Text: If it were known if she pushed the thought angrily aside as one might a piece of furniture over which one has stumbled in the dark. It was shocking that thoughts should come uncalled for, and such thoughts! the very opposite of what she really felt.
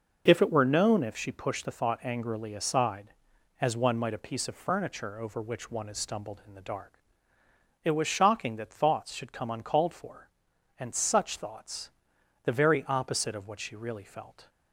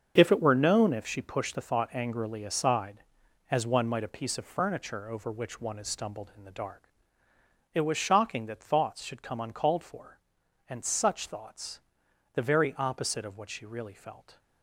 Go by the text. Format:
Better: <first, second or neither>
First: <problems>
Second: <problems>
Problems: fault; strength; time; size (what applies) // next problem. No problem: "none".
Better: first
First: none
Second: gets quieter; strong; throughout; 10 dB